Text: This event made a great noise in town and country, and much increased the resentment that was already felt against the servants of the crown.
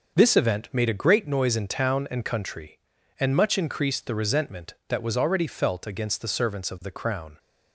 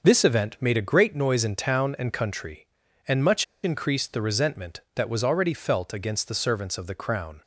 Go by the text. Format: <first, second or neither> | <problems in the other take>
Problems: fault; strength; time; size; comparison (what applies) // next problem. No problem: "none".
first | starts louder than the rest; until 1.0 s; 6 dB; also in the first // pauses between "much" and "increased"; slight; at 3.4 s; 0.19 s long